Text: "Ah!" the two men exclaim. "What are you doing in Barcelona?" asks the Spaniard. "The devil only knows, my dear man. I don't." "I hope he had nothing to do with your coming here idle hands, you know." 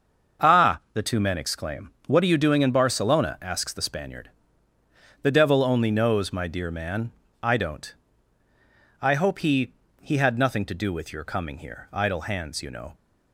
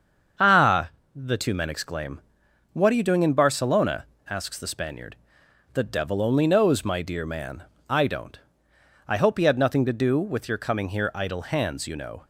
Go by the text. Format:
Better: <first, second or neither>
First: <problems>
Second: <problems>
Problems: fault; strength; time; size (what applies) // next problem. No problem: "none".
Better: second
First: starts louder than the rest; until 1.5 s; 6.5 dB // says "he" twice; at 10.0 s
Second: starts louder than the rest; until 1.6 s; 7 dB